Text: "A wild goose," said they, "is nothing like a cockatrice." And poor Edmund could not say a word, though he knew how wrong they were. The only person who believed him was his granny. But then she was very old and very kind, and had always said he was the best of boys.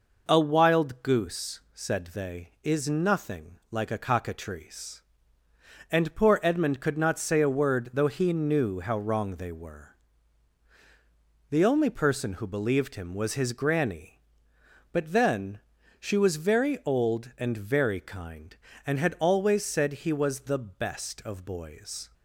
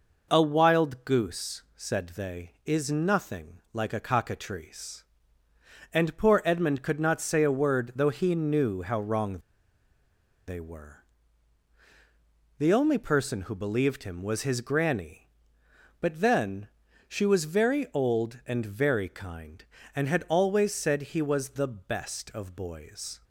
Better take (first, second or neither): first